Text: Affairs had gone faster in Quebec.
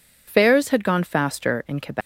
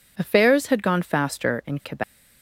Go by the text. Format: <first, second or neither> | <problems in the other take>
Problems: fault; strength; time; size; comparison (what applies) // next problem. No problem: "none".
second | loses the start of "Affairs"; at 0.2 s; 80 ms